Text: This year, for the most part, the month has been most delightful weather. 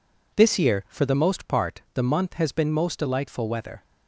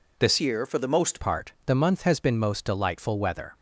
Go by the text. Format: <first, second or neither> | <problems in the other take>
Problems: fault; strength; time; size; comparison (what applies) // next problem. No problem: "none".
first | changes voice from "year" to "most"; from 0.3 to 1.1 s; 0.8 s long